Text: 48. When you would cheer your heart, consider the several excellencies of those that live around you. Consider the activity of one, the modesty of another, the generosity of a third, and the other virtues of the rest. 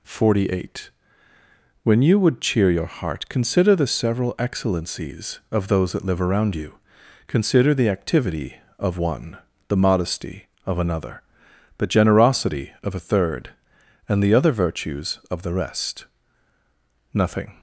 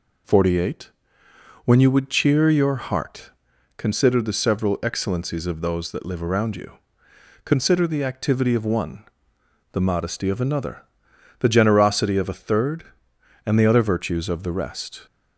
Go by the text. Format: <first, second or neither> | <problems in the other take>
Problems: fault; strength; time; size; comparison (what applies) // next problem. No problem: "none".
second | goes on to say "Nothing"; slight; from 17.1 s on; 0.44 s long